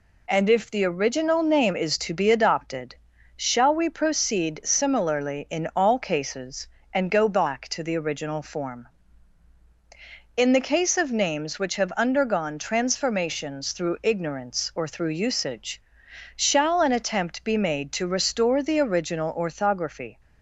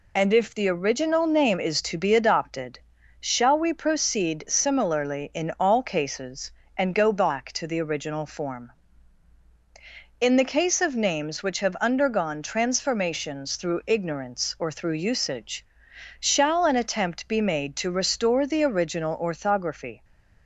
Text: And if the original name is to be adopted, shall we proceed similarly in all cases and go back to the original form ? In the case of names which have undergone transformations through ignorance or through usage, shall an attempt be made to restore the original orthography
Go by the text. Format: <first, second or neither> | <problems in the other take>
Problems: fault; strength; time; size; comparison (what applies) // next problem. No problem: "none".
first | loses the start of "And"; at 0.1 s; 35 ms // stays silent after the last word; slight; from 19.9 s on; 0.5 s long